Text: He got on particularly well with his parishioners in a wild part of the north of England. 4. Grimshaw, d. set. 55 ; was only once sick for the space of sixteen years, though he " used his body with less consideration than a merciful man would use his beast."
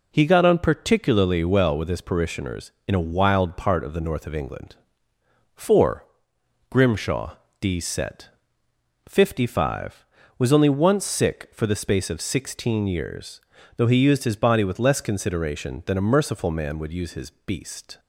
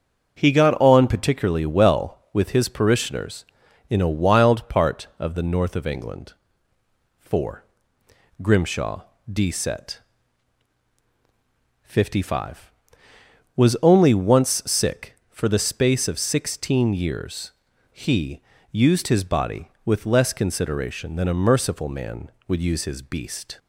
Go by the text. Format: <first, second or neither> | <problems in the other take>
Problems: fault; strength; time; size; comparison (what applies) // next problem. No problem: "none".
first | starts louder than the rest; until 1.3 s; 7 dB // skips "though"; at 17.7 s